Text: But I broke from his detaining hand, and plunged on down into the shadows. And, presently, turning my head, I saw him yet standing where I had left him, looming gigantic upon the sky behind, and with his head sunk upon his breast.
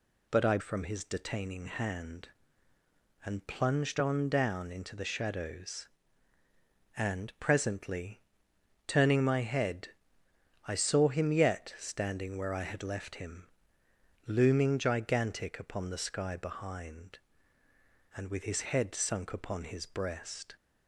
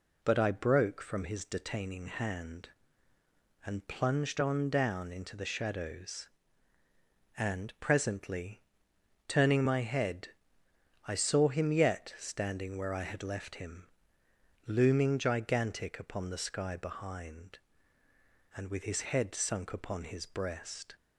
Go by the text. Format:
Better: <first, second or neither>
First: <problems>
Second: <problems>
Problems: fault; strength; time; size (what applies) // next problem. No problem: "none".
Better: second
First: skips "broke"; at 0.5 s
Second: none